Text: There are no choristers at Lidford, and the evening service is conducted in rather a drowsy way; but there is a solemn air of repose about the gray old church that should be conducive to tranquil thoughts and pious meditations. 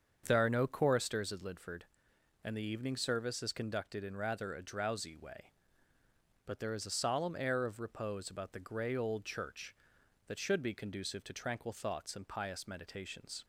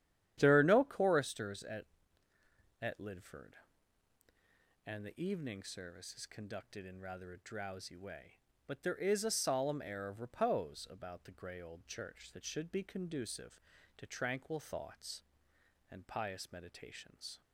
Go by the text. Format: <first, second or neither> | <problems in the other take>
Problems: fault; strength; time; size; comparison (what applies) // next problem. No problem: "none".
first | starts louder than the rest; strong; until 1.3 s; 11 dB; also in the first // says "at" twice; at 2.8 s